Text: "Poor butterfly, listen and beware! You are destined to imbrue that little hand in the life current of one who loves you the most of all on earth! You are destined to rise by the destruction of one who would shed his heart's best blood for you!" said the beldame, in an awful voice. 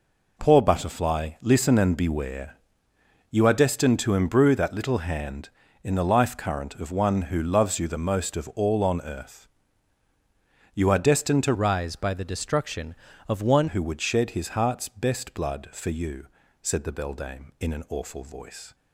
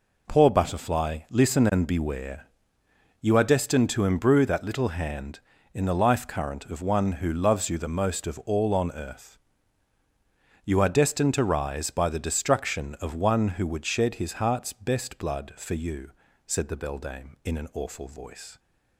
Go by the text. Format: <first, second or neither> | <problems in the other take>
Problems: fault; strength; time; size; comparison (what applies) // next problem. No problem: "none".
second | changes voice from "rise" to "one"; from 11.5 to 13.6 s; 2.1 s long